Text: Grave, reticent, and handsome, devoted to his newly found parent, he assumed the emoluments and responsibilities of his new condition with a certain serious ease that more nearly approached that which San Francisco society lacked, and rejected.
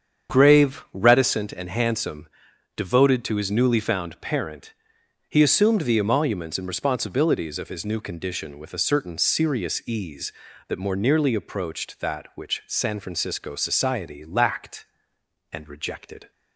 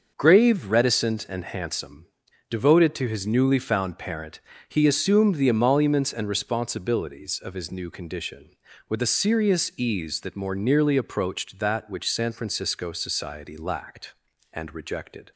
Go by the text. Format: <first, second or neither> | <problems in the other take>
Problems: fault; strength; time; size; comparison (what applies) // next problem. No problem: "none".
first | starts louder than the rest; until 1.1 s; 6.5 dB; strong in the first // skips "certain"; at 9.0 s